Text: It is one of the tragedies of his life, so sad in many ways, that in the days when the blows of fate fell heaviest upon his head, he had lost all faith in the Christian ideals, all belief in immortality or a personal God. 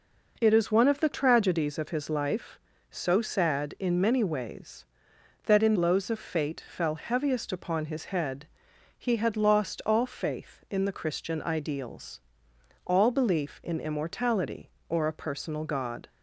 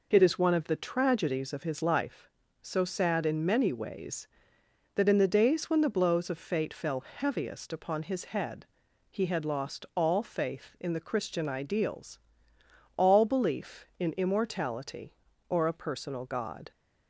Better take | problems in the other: second | skips "the days when the"; at 5.7 s

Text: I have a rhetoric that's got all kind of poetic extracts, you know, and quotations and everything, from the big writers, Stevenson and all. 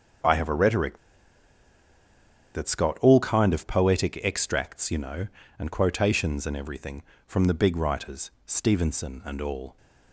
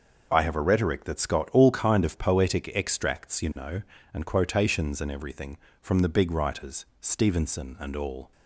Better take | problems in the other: second | pauses between "rhetoric" and "that's"; strong; at 0.9 s; 1.5 s long

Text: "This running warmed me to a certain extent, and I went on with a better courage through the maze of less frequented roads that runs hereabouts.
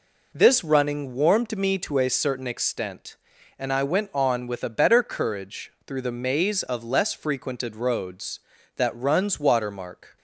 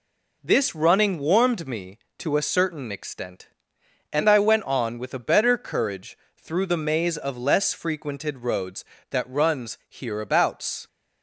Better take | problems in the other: second | pauses between "courage" and "through"; slight; at 5.7 s; 0.16 s long; slight in the second // says "watermark" for "hereabouts"; at 9.3 s

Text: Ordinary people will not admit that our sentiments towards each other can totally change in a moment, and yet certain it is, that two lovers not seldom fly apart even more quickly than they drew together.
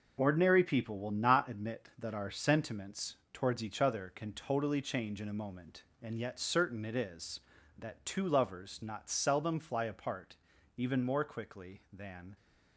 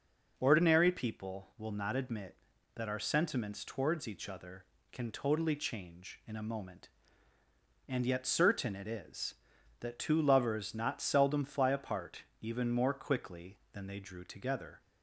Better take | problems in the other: second | pauses between "sentiments" and "towards"; slight; at 3.1 s; 0.16 s long // pauses between "apart" and "even"; at 10.3 s; 0.40 s long; slight in the second // stops before "they drew together"; at 12.3 s

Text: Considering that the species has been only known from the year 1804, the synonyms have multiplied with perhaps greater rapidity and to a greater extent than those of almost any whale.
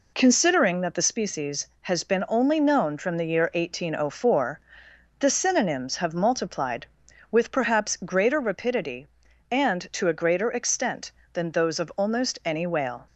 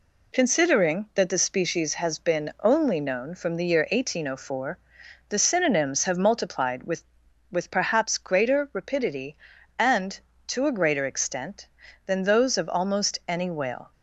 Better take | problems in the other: first | says "with" twice; at 7.4 s

